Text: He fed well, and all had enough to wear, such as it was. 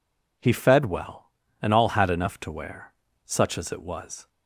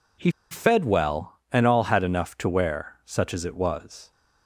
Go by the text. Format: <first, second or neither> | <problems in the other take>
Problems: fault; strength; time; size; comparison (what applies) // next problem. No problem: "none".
first | pauses between "He" and "fed"; slight; at 0.3 s; 0.19 s long